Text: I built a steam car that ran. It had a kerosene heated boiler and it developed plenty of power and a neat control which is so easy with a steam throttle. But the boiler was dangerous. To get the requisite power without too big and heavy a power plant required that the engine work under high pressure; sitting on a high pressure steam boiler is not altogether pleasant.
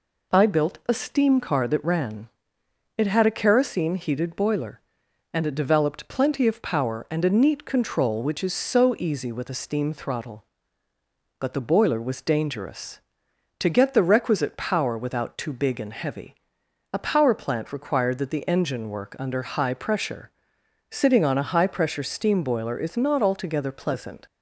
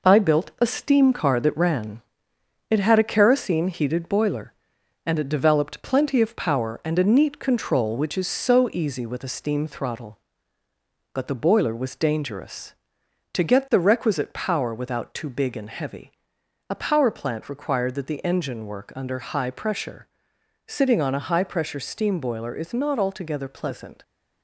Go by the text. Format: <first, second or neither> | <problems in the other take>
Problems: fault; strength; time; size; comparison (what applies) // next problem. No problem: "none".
first | gets quieter; noticeable; throughout; 5.5 dB // pauses between "heavy" and "a"; noticeable; at 16.1 s; 0.58 s long; noticeable in the first